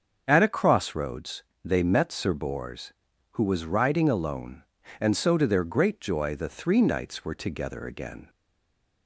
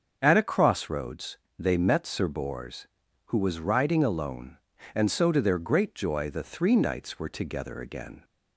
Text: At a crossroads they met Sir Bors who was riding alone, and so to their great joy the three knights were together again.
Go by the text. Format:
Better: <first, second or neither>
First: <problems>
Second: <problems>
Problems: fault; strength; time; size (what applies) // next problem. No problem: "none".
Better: second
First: starts louder than the rest; until 1.2 s; 7 dB // pauses between "crossroads" and "they"; slight; at 1.4 s; 0.22 s long // stays silent after the last word; slight; from 8.2 s on; 0.8 s long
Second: starts louder than the rest; until 1.2 s; 7 dB // pauses between "crossroads" and "they"; slight; at 1.3 s; 0.22 s long